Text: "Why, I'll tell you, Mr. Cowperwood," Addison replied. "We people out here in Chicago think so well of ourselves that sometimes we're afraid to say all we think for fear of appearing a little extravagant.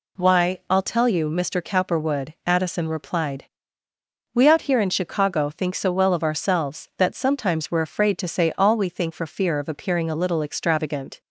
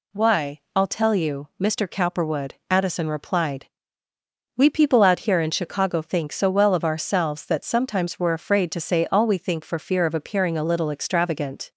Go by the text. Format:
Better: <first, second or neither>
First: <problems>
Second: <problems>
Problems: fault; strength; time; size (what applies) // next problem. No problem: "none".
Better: second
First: skips "people"; at 4.4 s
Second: none